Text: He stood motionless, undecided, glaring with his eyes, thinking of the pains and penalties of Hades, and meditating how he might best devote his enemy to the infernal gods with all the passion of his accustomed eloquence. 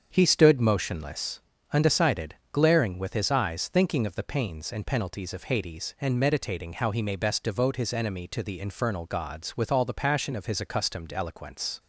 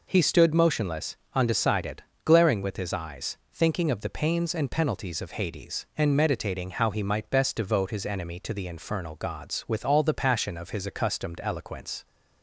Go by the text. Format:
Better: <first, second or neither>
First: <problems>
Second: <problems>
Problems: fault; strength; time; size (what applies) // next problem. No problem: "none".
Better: second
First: starts louder than the rest; strong; until 1.1 s; 7 dB // says "may" for "might"; at 7.0 s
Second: none